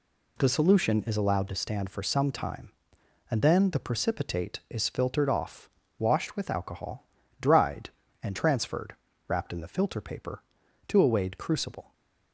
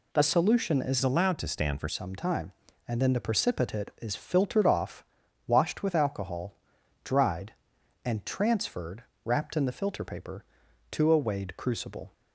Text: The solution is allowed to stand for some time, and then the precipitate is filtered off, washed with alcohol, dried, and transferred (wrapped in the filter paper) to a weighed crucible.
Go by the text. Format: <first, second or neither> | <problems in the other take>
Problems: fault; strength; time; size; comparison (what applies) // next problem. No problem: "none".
first | changes voice from "allowed" to "for"; from 1.0 to 1.8 s; 0.8 s long